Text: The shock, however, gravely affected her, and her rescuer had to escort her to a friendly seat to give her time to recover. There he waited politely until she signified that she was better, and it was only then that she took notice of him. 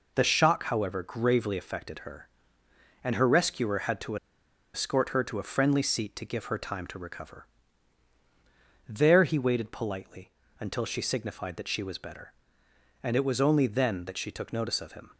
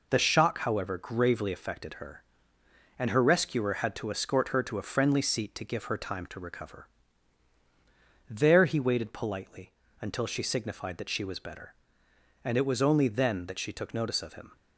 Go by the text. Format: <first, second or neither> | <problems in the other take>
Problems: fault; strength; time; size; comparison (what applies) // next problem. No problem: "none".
second | pauses between "to" and "escort"; noticeable; at 4.1 s; 0.58 s long // pauses between "politely" and "until"; slight; at 10.3 s; 0.28 s long; slight in the second